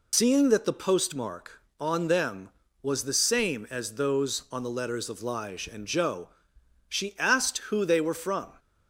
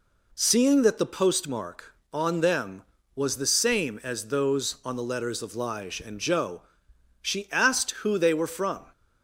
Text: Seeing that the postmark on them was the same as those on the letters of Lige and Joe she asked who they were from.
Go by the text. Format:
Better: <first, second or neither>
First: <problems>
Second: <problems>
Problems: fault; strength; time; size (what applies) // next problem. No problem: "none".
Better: second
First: loses the start of "Seeing"; at 0.1 s; 145 ms // pauses between "Joe" and "she"; noticeable; at 6.2 s; 0.62 s long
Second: pauses between "Joe" and "she"; noticeable; at 6.6 s; 0.62 s long